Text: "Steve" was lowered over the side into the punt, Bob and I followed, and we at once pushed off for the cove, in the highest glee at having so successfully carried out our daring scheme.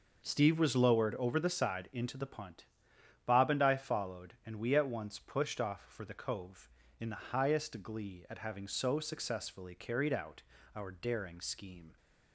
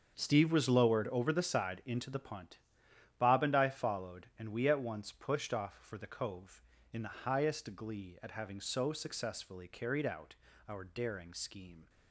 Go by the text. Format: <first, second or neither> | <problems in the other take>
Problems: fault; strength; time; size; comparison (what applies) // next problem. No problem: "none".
first | gets quieter; strong; throughout; 12.5 dB // pauses between "out" and "our"; slight; at 10.3 s; 0.34 s long; slight in the first